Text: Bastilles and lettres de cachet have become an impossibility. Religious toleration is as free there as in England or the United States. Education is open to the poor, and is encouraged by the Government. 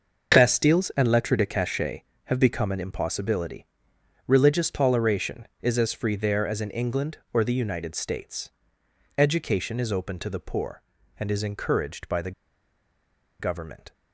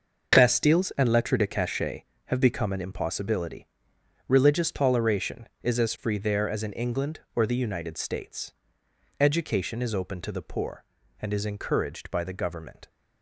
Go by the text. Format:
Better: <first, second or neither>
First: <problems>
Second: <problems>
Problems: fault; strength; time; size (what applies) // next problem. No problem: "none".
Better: second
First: starts louder than the rest; noticeable; until 1.3 s; 6 dB // pauses between "the" and "Government"; at 12.3 s; 1.0 s long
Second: starts louder than the rest; noticeable; until 1.4 s; 6 dB